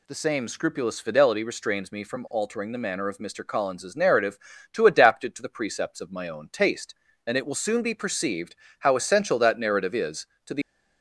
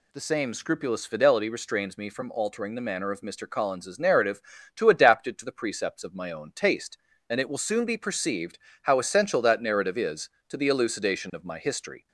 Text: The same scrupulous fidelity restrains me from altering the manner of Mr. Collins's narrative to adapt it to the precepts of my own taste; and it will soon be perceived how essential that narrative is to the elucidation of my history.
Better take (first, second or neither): second